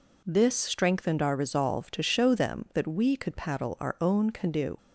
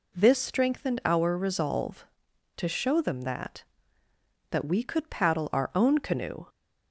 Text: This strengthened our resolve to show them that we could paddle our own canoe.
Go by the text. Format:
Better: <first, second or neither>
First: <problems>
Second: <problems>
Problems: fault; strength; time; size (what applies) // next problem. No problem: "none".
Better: first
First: none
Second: says "that" twice; at 4.5 s